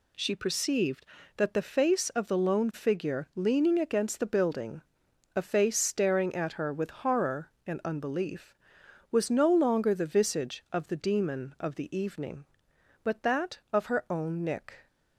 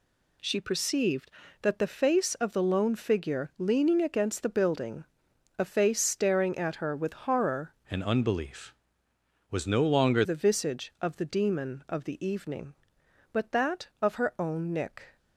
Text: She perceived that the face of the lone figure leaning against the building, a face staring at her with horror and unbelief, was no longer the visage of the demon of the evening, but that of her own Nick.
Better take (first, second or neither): first